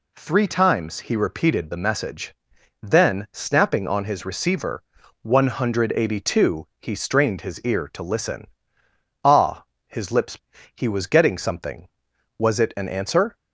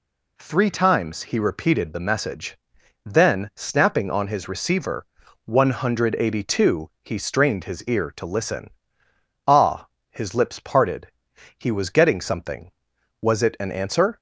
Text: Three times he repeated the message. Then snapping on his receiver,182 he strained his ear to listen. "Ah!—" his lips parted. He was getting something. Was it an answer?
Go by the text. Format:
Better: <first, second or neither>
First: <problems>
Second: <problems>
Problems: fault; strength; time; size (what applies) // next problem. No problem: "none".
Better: second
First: skips "parted"; at 10.5 s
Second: none